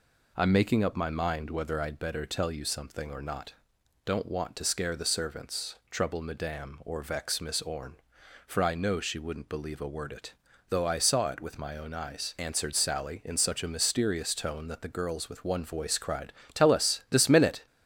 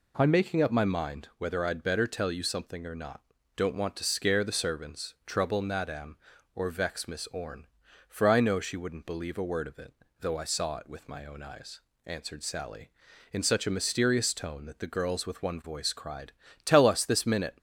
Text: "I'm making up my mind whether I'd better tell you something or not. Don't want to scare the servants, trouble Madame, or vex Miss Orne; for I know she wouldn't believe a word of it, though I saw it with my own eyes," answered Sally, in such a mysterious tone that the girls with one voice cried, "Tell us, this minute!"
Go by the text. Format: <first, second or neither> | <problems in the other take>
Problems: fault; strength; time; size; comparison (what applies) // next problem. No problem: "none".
second | skips "of"; at 10.1 s